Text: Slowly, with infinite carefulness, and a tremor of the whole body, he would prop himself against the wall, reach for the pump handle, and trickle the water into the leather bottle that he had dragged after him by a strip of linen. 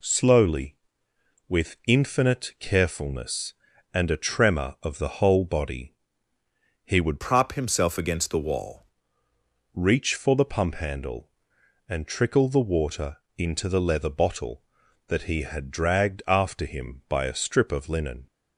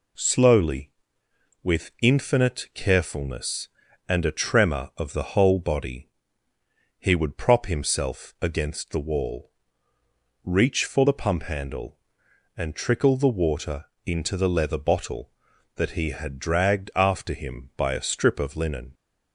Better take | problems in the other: second | changes voice from "prop" to "wall"; from 7.2 to 8.8 s; 1.6 s long // pauses between "water" and "into"; slight; at 13.1 s; 0.18 s long; slight in the second

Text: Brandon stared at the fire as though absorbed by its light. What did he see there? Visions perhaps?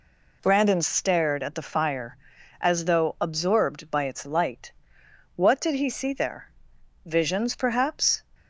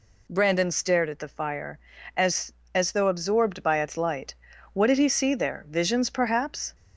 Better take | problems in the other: first | says "as" twice; at 2.7 s

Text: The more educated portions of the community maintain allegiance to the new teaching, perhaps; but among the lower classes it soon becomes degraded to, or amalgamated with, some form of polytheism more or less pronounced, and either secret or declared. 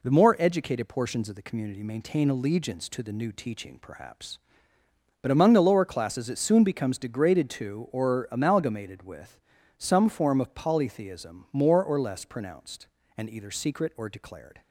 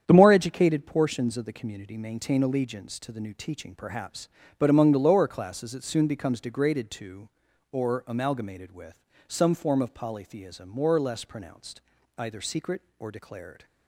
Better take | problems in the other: first | starts louder than the rest; strong; until 1.0 s; 8.5 dB // skips "and"; at 11.9 s

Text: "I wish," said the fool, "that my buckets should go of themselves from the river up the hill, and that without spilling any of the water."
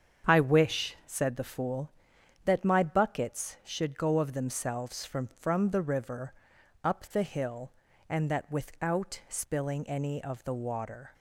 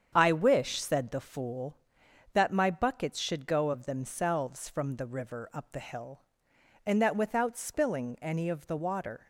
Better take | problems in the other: second | starts louder than the rest; strong; until 1.3 s; 7.5 dB; strong in the second // says "from" twice; at 5.2 s // pauses between "river" and "up"; noticeable; at 6.3 s; 0.50 s long

